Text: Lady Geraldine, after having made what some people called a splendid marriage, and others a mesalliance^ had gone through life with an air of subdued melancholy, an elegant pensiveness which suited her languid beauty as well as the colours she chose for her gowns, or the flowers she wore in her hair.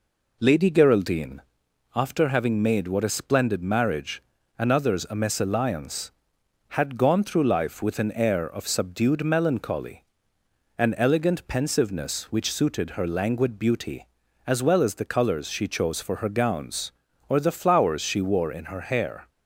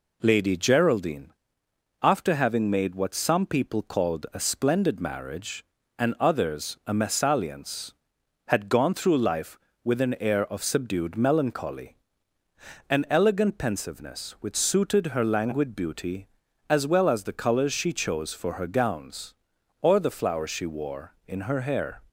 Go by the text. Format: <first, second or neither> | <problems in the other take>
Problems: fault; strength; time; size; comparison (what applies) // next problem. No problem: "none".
second | skips "some people called"; at 3.0 s